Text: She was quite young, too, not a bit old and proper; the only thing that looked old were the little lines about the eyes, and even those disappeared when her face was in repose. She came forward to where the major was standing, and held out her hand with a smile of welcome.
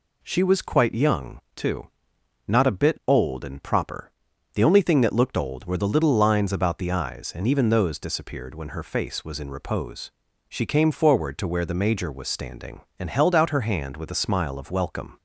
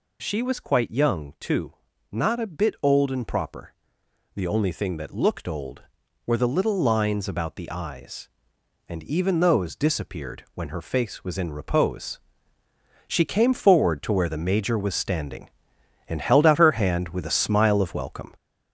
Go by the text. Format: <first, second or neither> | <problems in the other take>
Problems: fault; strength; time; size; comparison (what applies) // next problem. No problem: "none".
first | gets louder; noticeable; throughout; 4 dB